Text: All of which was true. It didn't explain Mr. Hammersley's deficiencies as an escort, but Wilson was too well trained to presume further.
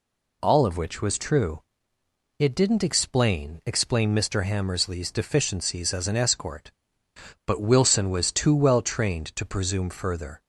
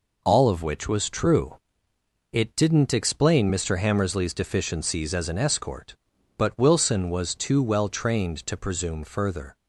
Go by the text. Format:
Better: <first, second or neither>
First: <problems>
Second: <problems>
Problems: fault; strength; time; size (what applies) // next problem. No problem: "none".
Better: second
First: says "explain" twice; at 3.6 s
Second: none